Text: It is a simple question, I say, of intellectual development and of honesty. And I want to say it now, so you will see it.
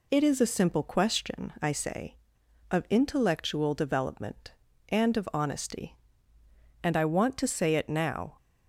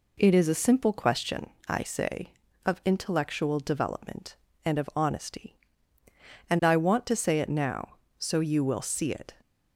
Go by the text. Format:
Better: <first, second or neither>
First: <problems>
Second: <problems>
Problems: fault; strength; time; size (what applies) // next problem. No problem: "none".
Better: second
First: stops before "so you will see it"; at 8.3 s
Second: none